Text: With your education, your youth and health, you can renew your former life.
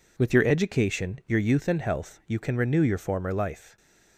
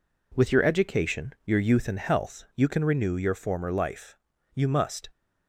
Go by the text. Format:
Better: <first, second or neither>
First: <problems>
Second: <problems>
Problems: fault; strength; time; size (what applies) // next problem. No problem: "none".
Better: first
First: none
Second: goes on to say "You must"; from 4.5 s on; 0.56 s long